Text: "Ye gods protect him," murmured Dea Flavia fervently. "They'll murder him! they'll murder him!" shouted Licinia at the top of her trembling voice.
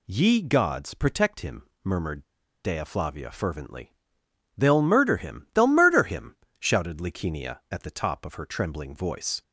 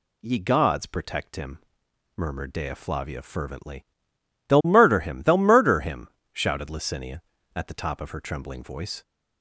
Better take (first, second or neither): second